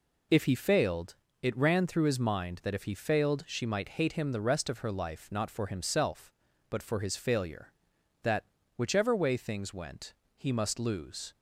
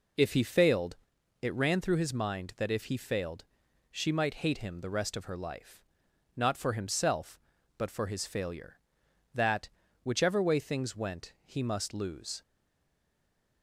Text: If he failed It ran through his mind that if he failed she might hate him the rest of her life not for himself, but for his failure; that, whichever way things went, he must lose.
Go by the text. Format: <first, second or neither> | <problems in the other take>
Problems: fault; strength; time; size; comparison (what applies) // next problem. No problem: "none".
first | pauses between "failed" and "It"; at 0.9 s; 0.44 s long; slight in the first // pauses between "failed" and "she"; at 3.4 s; 0.44 s long // pauses between "life" and "not"; noticeable; at 5.8 s; 0.52 s long // stays silent after the last word; noticeable; from 12.4 s on; 1.2 s long